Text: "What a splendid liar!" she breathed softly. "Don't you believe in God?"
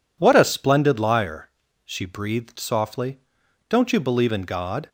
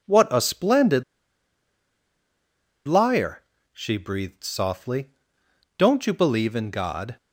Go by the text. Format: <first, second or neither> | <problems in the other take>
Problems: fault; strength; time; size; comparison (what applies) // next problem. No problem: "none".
first | pauses between "splendid" and "liar"; strong; at 1.0 s; 1.8 s long